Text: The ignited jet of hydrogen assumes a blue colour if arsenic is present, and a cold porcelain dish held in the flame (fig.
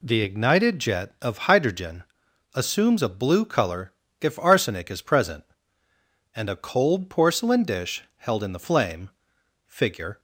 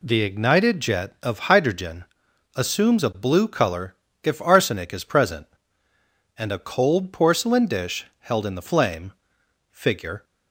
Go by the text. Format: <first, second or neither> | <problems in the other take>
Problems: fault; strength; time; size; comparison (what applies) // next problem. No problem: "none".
neither | pauses between "hydrogen" and "assumes"; noticeable; the same in both // pauses between "colour" and "if"; slight; the same in both